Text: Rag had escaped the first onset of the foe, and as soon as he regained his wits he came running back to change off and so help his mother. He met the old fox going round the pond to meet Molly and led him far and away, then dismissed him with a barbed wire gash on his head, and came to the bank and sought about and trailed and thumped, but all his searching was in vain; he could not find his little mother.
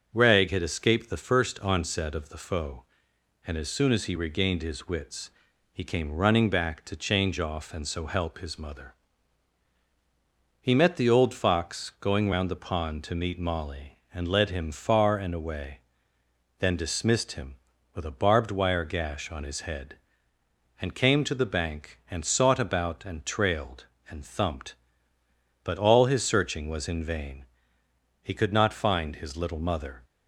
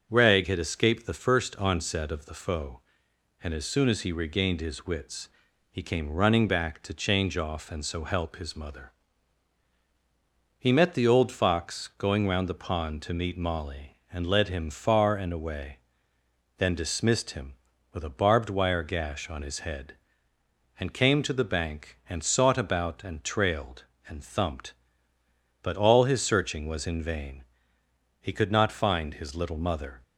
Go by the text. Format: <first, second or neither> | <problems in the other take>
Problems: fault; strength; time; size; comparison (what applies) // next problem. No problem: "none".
neither | starts louder than the rest; the same in both // pauses between "wits" and "he"; the same in both